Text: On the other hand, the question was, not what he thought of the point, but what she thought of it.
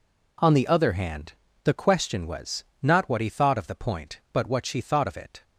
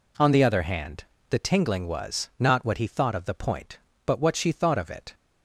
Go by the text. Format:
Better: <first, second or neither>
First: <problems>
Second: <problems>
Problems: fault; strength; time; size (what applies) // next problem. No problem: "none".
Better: first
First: none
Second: says "tingling" for "question"; at 1.3 s